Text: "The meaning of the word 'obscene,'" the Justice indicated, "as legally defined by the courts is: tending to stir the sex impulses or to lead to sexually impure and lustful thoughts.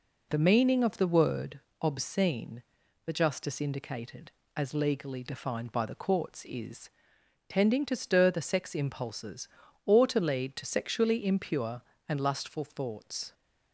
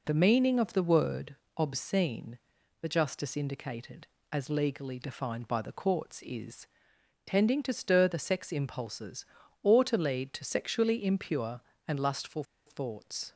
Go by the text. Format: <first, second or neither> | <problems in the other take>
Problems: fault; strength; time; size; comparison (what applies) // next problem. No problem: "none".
first | pauses between "word" and "obscene"; slight; at 1.3 s; 0.22 s long; slight in the first // pauses between "lustful" and "thoughts"; slight; at 12.4 s; 0.24 s long